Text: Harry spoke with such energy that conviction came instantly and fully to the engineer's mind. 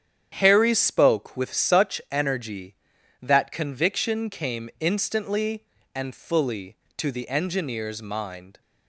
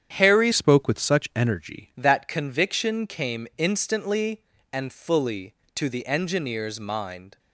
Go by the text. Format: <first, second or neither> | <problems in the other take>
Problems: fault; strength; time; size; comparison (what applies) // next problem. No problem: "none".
first | starts louder than the rest; strong; until 1.1 s; 9 dB; strong in the first // changes voice from "spoke" to "energy"; from 0.5 to 1.9 s; 1.4 s long